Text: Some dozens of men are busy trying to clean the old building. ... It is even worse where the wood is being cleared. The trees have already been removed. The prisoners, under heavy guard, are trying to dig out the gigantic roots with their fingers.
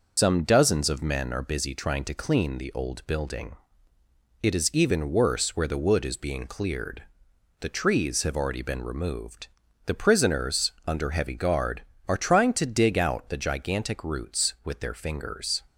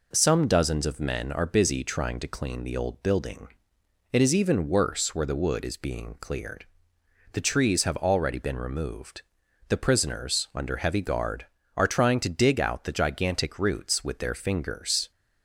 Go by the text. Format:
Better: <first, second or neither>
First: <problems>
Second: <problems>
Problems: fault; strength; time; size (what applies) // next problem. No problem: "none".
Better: second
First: loses the start of "Some"; at 0.1 s; 105 ms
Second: none